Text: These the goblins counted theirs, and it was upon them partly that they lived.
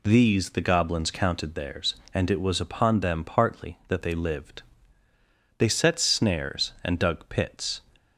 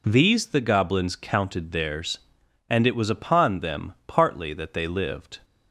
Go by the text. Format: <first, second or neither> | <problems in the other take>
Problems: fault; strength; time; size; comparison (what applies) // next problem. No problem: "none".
second | goes on to say "They set snares and dug pits"; strong; from 5.5 s on; 2.2 s long